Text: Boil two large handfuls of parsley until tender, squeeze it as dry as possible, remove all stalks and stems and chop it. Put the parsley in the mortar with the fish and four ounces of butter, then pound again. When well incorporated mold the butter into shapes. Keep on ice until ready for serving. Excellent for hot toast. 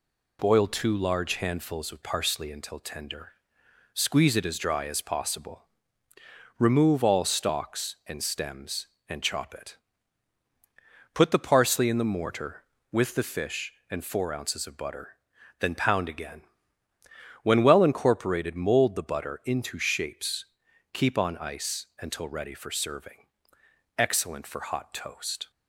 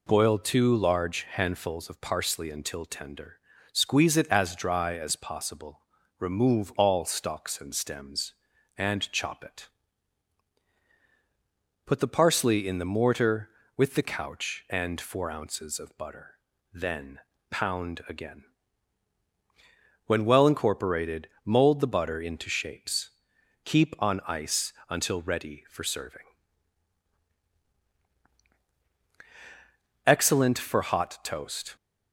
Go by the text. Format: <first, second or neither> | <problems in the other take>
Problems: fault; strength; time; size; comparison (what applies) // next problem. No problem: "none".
first | says "couch" for "fish"; at 14.0 s // pauses between "then" and "pound"; slight; at 17.1 s; 0.30 s long // pauses between "incorporated" and "mold"; slight; at 21.2 s; 0.16 s long // pauses between "ice" and "until"; slight; at 24.7 s; 0.16 s long